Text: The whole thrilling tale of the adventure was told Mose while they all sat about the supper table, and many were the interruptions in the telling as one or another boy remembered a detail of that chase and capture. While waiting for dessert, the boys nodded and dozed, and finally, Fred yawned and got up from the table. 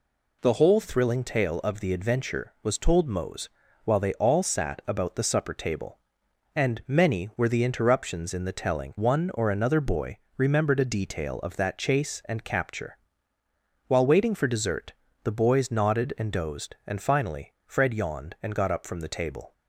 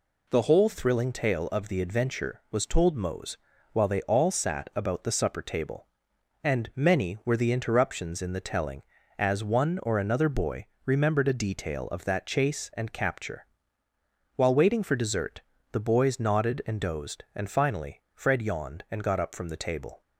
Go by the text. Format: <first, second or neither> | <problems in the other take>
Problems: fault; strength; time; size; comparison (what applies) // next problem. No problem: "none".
second | pauses between "Mose" and "while"; slight; at 3.4 s; 0.36 s long; slight in the second // skips "as"; at 8.9 s // pauses between "boy" and "remembered"; slight; at 10.1 s; 0.20 s long; slight in the second